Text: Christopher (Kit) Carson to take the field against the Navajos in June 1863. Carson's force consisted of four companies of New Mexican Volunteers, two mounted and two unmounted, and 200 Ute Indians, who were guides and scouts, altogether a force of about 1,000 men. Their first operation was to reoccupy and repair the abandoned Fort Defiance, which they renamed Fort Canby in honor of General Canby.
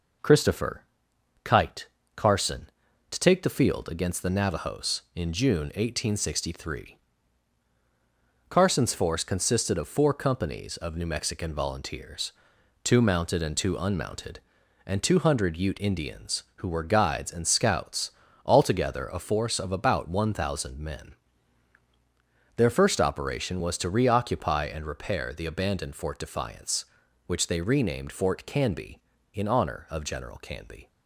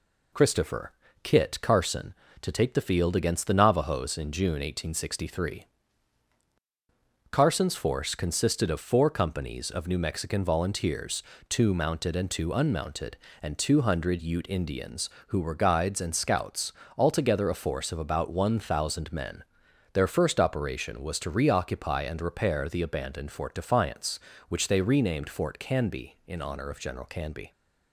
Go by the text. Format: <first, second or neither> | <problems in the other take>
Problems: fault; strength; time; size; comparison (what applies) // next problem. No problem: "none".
second | says "Kite" for "Kit"; at 1.4 s